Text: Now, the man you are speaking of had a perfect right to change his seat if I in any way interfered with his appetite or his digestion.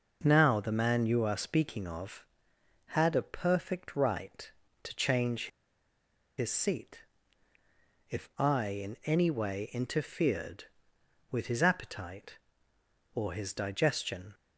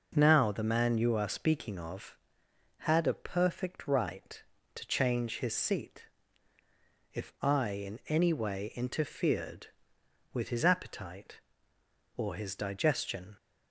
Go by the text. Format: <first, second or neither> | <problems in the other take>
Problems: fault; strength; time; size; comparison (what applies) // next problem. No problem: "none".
second | pauses between "change" and "his"; noticeable; at 5.4 s; 0.90 s long // pauses between "seat" and "if"; at 7.0 s; 1.0 s long; also in the second